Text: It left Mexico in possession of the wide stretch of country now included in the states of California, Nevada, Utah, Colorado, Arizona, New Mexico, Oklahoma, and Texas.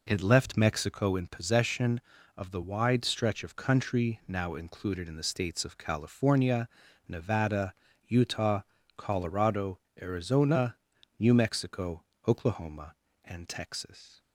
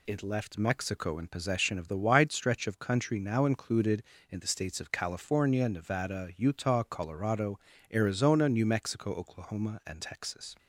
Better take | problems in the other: neither | none

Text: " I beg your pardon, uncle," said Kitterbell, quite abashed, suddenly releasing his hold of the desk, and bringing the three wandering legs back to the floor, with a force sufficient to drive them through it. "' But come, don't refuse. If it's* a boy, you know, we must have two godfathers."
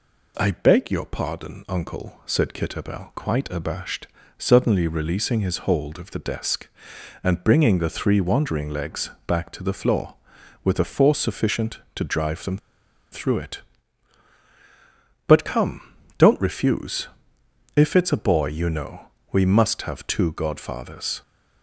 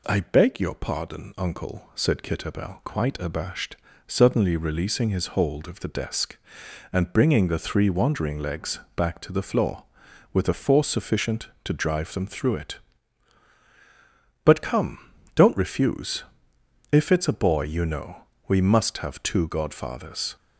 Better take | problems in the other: second | pauses between "legs" and "back"; slight; at 9.1 s; 0.16 s long; slight in the second // pauses between "them" and "through"; noticeable; at 12.5 s; 0.54 s long

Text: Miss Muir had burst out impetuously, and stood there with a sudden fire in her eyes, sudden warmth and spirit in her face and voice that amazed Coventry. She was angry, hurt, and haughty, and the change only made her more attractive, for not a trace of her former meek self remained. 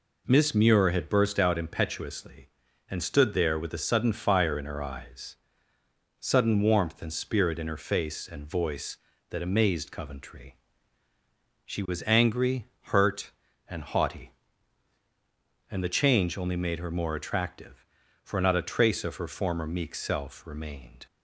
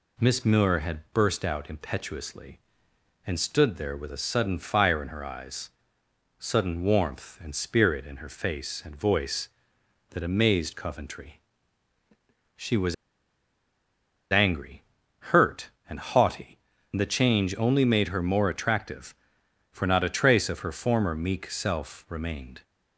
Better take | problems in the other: first | pauses between "was" and "angry"; strong; at 12.9 s; 1.3 s long

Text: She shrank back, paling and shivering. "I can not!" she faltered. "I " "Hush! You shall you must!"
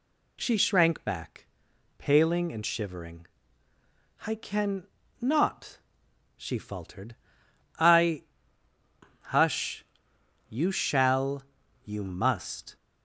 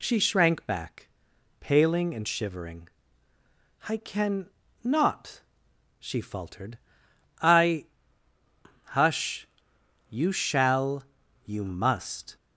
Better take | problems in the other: neither | pauses between "can" and "not"; slight; the same in both // pauses between "shall" and "you"; the same in both

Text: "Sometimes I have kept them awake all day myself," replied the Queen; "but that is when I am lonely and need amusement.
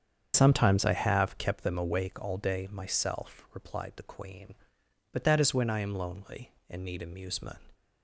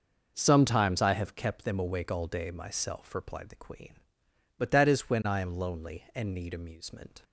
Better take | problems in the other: second | starts louder than the rest; strong; until 1.6 s; 7.5 dB

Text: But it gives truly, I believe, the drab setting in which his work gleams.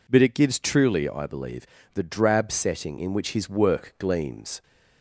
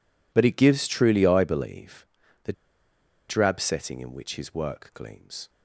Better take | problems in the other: first | pauses between "the" and "drab"; noticeable; at 2.5 s; 0.76 s long

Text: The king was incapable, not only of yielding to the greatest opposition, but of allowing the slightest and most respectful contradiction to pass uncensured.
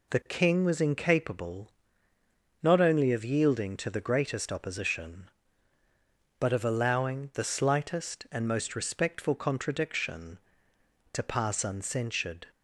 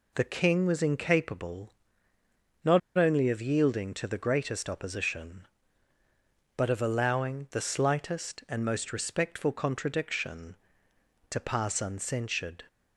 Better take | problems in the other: first | pauses between "not" and "only"; slight; at 2.7 s; 0.18 s long

